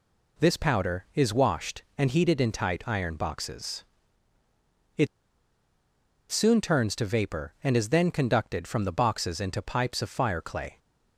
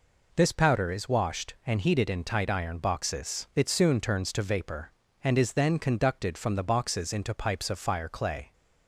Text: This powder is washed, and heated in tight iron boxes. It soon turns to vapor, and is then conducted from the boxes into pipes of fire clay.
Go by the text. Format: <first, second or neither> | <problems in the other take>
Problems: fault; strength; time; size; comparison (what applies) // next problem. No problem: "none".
second | pauses between "It" and "soon"; strong; at 5.0 s; 1.2 s long